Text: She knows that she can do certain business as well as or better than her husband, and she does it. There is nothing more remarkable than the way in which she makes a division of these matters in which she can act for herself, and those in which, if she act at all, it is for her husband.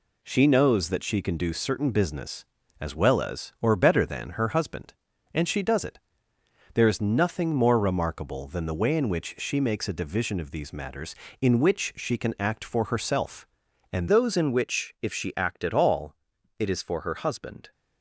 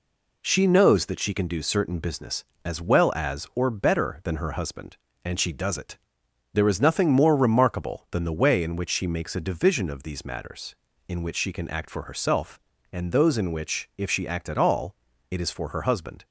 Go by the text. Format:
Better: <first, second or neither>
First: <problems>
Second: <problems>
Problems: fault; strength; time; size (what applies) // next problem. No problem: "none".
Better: second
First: changes voice at "those"; from 14.0 s on; 3.7 s long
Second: none